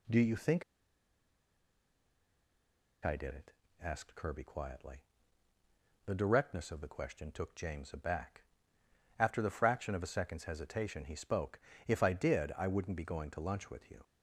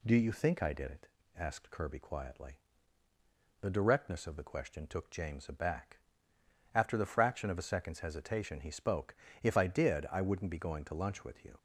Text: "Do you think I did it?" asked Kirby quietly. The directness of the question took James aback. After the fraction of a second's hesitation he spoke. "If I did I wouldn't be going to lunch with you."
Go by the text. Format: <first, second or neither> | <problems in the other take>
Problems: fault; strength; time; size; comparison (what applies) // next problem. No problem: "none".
second | pauses between "think" and "I"; strong; at 0.6 s; 2.4 s long